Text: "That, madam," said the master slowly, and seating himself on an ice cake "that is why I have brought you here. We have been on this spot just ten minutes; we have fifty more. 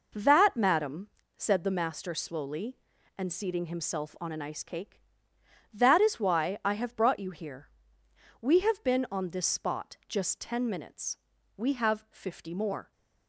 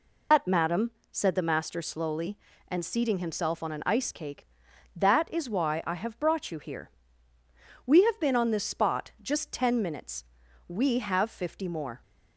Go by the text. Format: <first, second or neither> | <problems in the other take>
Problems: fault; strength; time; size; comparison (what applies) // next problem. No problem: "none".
first | loses the start of "That"; at 0.3 s; 105 ms